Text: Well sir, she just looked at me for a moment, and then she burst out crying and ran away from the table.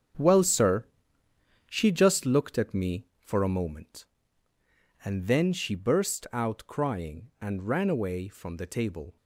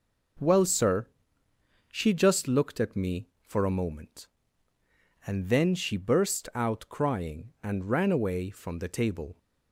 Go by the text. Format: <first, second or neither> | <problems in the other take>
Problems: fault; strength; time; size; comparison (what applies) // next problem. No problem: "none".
second | gets quieter; strong; throughout; 10 dB